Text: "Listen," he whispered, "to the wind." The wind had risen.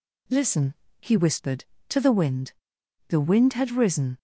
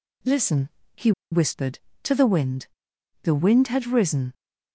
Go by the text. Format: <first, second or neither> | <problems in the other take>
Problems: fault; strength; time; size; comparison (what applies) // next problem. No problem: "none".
first | pauses between "he" and "whispered"; slight; at 1.1 s; 0.20 s long